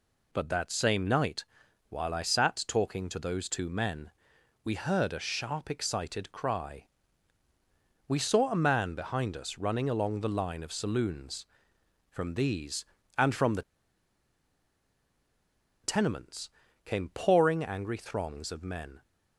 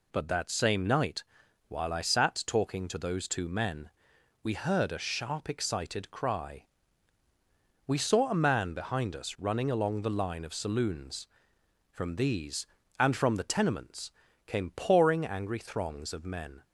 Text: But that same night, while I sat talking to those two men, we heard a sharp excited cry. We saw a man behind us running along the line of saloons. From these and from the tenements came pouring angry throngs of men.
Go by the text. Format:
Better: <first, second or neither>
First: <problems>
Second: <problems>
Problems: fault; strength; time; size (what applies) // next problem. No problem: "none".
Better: second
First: pauses between "the" and "tenements"; strong; at 13.6 s; 2.2 s long // pauses between "tenements" and "came"; slight; at 16.5 s; 0.34 s long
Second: pauses between "tenements" and "came"; slight; at 14.1 s; 0.34 s long